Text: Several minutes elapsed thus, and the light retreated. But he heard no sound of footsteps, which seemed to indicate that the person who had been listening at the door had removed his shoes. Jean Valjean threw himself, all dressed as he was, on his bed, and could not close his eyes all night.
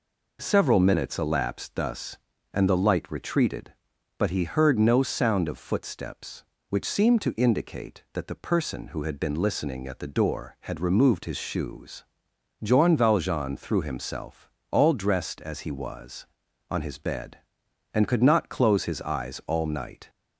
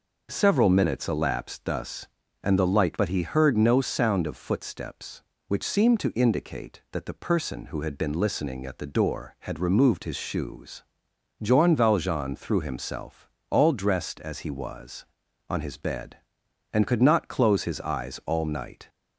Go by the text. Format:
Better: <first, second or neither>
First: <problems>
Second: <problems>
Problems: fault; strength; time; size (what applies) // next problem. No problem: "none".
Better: first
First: none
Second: skips "retreated"; at 2.9 s